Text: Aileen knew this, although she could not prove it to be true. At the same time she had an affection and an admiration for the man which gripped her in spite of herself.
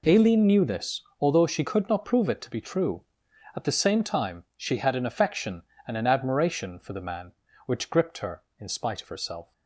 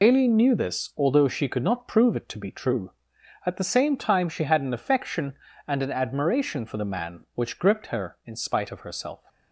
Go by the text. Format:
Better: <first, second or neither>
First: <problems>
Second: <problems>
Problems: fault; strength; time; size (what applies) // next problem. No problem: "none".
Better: first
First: none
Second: loses the start of "Aileen"; at 0.0 s; 50 ms